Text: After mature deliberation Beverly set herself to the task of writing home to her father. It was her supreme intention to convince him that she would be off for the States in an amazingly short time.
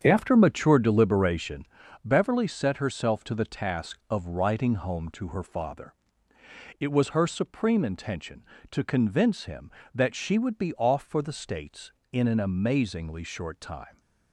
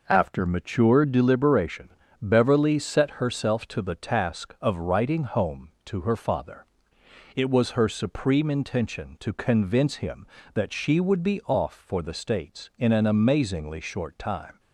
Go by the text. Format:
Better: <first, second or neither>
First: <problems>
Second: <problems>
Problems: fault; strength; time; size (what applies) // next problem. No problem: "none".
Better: second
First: starts louder than the rest; strong; until 1.9 s; 8 dB // pauses between "deliberation" and "Beverly"; at 1.6 s; 0.40 s long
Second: pauses between "deliberation" and "Beverly"; slight; at 1.8 s; 0.32 s long